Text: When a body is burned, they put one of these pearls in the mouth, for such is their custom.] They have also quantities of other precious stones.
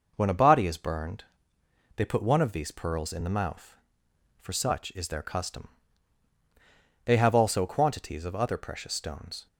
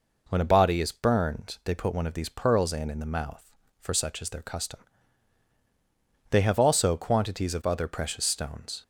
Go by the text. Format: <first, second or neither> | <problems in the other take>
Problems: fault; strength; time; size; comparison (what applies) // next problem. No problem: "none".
first | says "in" twice; at 2.8 s